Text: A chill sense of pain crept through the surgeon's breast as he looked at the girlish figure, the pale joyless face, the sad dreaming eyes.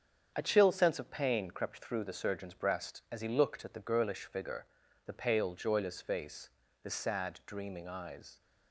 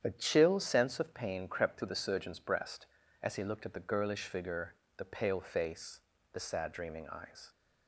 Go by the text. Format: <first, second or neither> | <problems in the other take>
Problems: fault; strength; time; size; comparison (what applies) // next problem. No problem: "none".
first | starts louder than the rest; strong; until 1.0 s; 9 dB; strong in the first // skips "joyless"; at 5.4 s